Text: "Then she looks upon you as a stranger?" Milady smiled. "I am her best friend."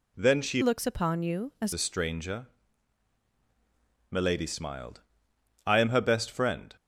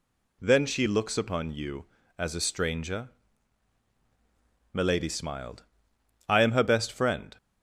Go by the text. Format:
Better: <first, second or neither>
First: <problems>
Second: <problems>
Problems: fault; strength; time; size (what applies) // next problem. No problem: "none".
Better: second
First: changes voice from "looks" to "as"; from 0.6 to 1.7 s; 1.1 s long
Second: none